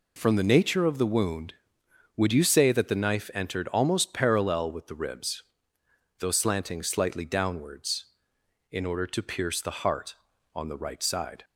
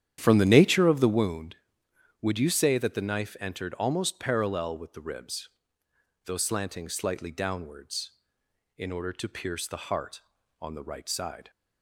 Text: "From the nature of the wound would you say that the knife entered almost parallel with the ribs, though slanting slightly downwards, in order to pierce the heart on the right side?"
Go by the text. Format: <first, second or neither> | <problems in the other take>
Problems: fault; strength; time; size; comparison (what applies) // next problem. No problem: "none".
first | starts louder than the rest; strong; until 1.3 s; 10 dB